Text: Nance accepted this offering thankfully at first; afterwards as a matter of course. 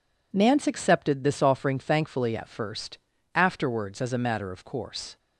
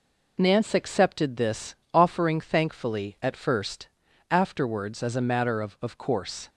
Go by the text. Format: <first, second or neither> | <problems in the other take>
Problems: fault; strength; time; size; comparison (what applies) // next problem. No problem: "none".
first | pauses between "this" and "offering"; slight; at 1.7 s; 0.18 s long // says "of" twice; at 5.8 s